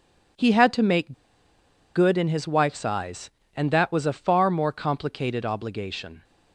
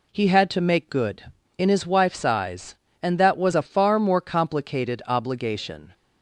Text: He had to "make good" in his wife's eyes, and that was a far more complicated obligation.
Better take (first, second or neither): second